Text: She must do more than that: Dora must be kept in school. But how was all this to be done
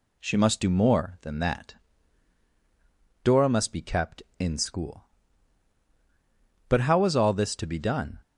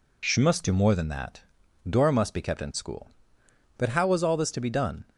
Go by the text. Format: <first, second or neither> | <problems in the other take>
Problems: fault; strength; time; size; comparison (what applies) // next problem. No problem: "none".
neither | none